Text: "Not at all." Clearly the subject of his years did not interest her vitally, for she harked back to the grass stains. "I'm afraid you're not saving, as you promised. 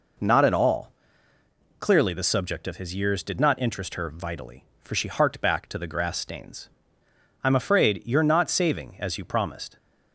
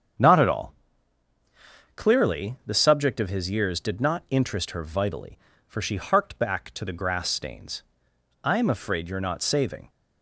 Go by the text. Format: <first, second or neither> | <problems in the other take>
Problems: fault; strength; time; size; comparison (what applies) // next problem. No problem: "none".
first | starts louder than the rest; strong; until 2.3 s; 7.5 dB // stops before "as you promised"; at 9.8 s